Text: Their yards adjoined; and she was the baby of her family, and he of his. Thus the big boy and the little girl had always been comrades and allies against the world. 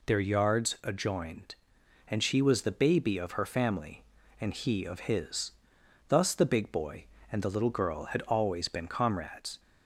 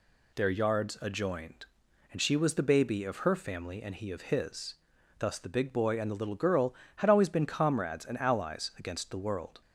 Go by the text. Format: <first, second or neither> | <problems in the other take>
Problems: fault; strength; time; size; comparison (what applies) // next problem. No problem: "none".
second | stops before "and allies against the world"; at 9.5 s